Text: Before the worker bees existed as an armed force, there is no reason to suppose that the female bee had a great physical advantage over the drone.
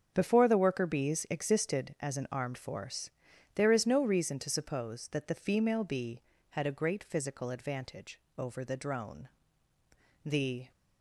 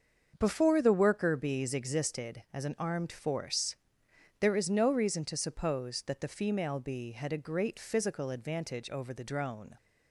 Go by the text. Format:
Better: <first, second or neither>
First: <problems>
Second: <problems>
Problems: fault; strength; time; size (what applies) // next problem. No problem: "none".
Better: second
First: starts louder than the rest; strong; until 1.1 s; 7.5 dB // goes on to say "The"; slight; from 10.2 s on; 0.46 s long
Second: starts louder than the rest; until 1.4 s; 6.5 dB